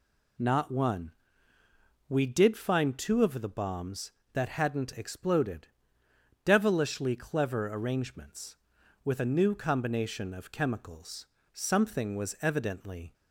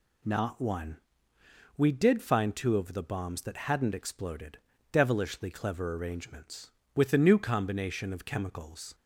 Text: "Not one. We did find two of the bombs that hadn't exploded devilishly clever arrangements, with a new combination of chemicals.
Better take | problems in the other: second | pauses between "exploded" and "devilishly"; noticeable; at 5.6 s; 0.78 s long; slight in the second // goes on to say "Something was evidently"; from 11.5 s on; 1.6 s long

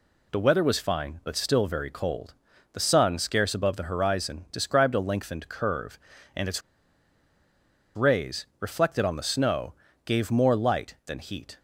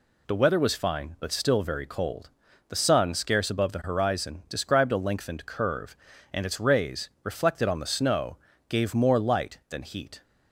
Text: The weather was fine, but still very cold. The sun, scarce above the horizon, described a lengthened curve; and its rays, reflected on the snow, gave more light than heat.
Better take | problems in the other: second | pauses between "its" and "rays"; strong; at 6.6 s; 1.3 s long

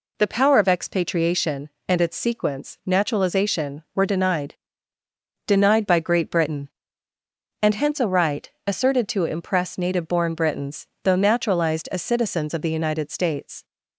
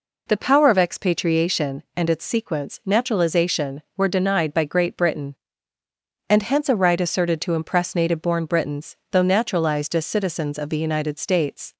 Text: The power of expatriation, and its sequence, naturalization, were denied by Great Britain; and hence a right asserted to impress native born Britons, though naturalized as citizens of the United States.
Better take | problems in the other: second | says "denied" twice; at 5.4 s // pauses between "right" and "asserted"; slight; at 8.4 s; 0.16 s long

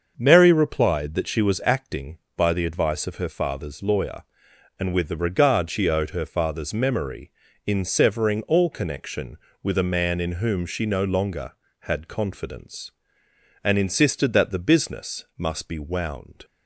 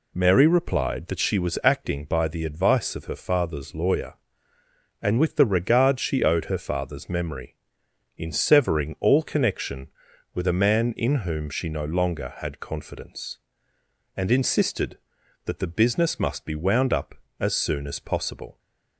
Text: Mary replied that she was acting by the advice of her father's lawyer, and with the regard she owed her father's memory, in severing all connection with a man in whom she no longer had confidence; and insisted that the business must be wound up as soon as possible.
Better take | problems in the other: second | starts louder than the rest; until 1.1 s; 6.5 dB // stops before "up as soon as possible"; at 16.4 s

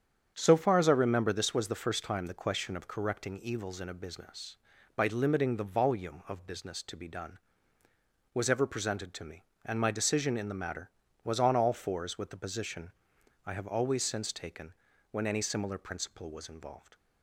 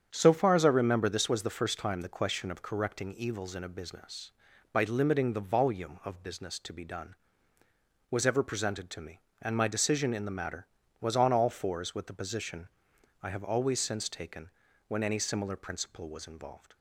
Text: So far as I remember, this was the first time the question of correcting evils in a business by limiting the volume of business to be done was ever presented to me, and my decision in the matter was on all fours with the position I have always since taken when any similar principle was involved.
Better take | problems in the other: neither | starts louder than the rest; strong; the same in both // pauses between "position" and "I"; noticeable; the same in both // pauses between "taken" and "when"; the same in both

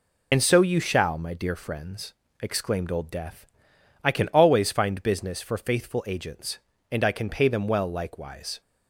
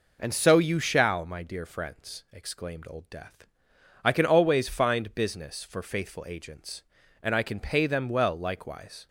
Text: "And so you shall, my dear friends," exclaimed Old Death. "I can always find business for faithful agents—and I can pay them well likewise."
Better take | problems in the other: second | loses the start of "And"; at 0.3 s; 55 ms

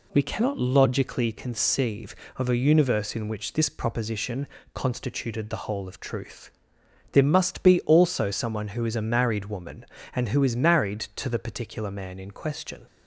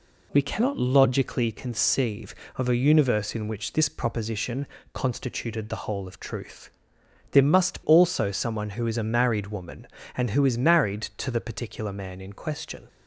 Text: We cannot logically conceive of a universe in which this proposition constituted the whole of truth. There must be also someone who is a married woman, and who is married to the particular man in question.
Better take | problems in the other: first | pauses between "proposition" and "constituted"; slight; at 4.6 s; 0.26 s long; slight in the first // skips "be"; at 7.8 s

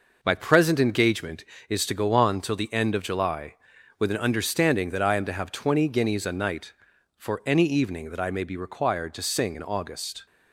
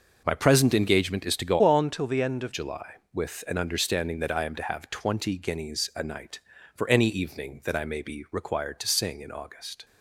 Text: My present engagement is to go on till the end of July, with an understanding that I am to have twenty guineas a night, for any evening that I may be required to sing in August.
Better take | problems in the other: first | changes voice from "on" to "of"; from 1.6 to 2.5 s; 0.9 s long

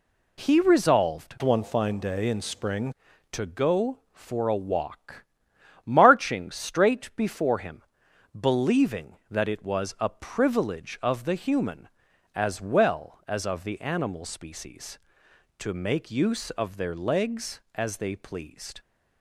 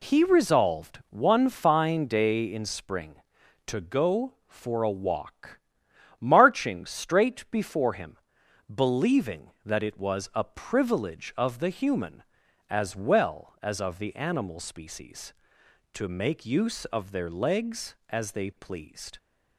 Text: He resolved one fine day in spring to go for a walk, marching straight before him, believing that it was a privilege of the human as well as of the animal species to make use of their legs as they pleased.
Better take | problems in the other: second | changes voice from "one" to "spring"; from 1.4 to 2.9 s; 1.5 s long

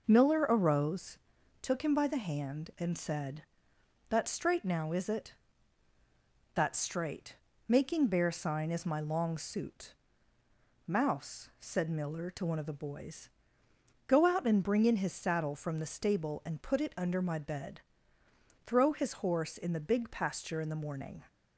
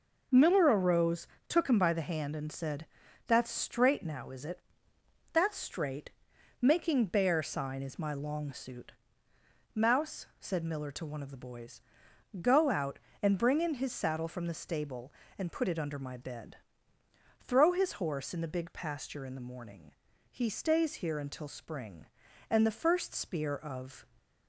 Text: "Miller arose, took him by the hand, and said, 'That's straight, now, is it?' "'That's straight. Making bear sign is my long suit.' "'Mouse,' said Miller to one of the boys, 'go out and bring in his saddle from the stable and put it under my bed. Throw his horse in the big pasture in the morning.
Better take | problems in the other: first | goes on to say "He stays here until spring and the first spear of"; strong; from 20.3 s on; 3.7 s long

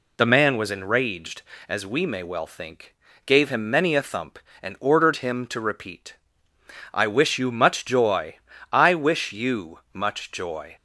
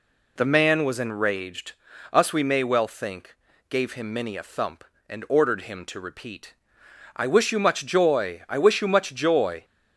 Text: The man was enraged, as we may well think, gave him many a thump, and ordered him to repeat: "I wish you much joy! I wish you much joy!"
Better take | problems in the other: first | says "us" for "as"; at 2.1 s

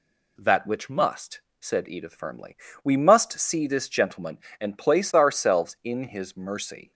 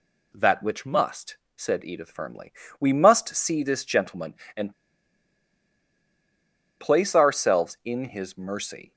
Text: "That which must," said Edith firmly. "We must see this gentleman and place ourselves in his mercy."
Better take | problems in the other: first | pauses between "and" and "place"; strong; at 4.7 s; 2.0 s long

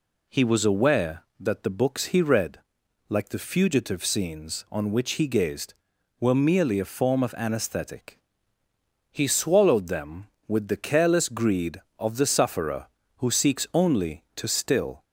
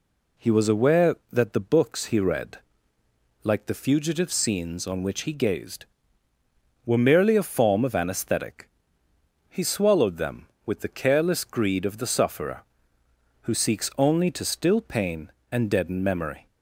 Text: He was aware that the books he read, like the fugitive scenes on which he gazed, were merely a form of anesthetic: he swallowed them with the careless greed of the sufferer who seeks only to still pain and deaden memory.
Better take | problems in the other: second | stops before "pain and deaden memory"; at 15.0 s

